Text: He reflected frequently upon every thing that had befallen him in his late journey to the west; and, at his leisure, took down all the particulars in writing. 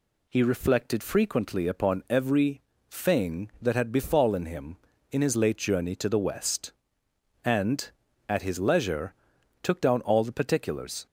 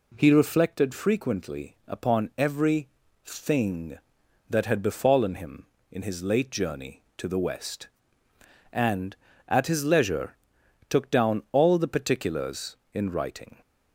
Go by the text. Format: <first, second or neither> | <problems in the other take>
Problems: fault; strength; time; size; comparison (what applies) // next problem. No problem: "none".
second | pauses between "every" and "thing"; slight; at 2.6 s; 0.28 s long; slight in the second // stops before "in writing"; at 11.0 s